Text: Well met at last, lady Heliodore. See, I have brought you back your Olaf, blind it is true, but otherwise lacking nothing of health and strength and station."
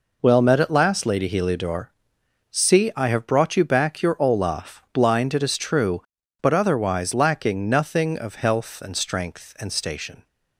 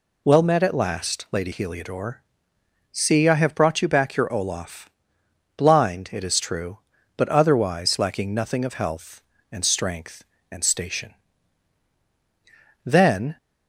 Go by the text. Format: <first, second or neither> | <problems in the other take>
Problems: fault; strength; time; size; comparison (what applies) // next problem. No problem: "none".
first | goes on to say "Then"; from 12.8 s on; 0.52 s long